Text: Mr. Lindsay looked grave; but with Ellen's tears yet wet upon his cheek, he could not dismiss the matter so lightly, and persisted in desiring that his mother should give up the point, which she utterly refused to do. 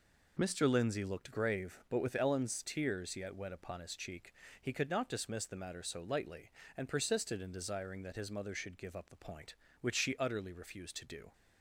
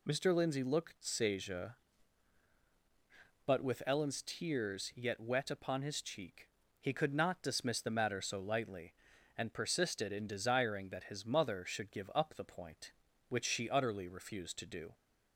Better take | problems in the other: first | says "seja" for "grave"; at 1.0 s

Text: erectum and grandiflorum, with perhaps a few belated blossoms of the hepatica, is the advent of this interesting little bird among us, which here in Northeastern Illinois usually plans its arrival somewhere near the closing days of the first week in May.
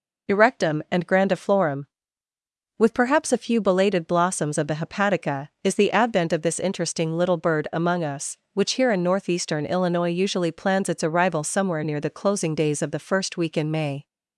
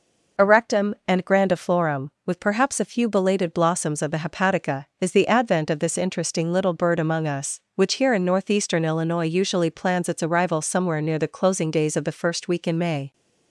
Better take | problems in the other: neither | none

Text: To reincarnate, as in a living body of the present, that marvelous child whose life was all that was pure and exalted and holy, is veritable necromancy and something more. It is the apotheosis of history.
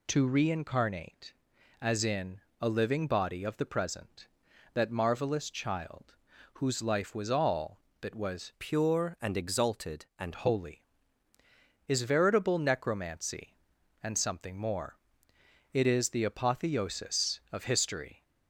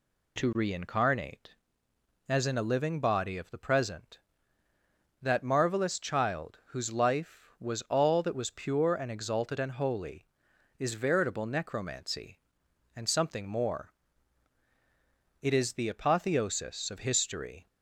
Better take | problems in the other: second | pauses between "in" and "a"; slight; at 2.4 s; 0.18 s long // pauses between "child" and "whose"; at 6.1 s; 0.40 s long // changes voice from "pure" to "and"; from 8.5 to 10.3 s; 1.8 s long

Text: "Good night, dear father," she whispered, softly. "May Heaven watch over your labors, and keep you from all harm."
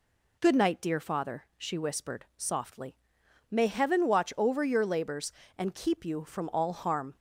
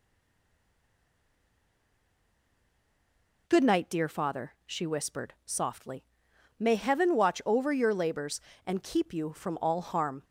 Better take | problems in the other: first | stays silent before the first word; strong; until 3.4 s; 3.4 s long

